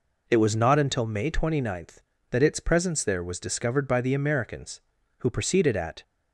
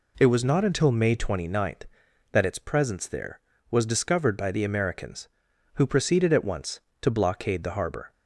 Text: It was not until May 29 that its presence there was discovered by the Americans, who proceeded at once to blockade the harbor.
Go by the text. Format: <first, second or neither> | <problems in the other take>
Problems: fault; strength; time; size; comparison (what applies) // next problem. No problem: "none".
second | stops before "once to blockade the harbor"; at 6.0 s